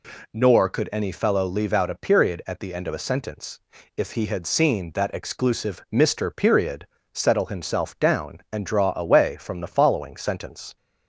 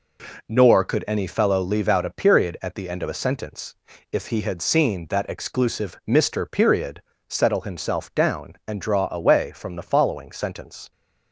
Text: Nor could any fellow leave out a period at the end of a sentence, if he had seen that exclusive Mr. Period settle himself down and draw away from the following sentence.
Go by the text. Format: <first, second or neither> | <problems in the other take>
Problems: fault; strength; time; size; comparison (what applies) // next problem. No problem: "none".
first | gets quieter; throughout; 6.5 dB // pauses between "Period" and "settle"; slight; at 7.0 s; 0.26 s long; slight in the first